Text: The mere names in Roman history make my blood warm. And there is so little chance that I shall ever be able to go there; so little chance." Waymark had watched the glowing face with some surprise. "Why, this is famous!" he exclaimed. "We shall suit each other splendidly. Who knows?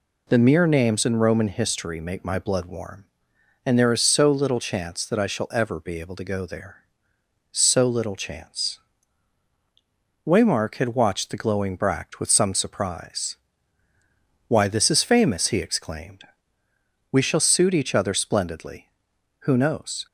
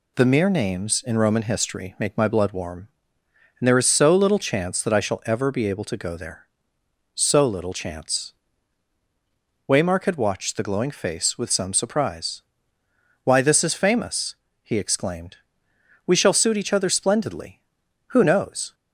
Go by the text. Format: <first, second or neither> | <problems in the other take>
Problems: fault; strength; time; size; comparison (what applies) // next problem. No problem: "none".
second | says "bract" for "face"; at 11.7 s